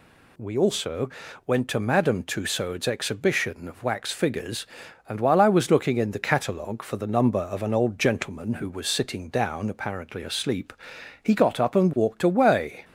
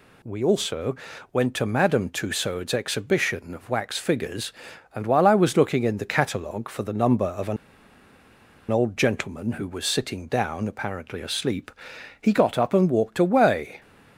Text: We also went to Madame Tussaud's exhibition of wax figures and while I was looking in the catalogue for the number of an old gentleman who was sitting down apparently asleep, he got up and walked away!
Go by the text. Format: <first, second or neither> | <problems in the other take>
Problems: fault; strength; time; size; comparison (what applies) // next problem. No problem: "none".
first | pauses between "also" and "went"; at 0.9 s; 0.38 s long; also in the first // pauses between "an" and "old"; at 7.5 s; 1.1 s long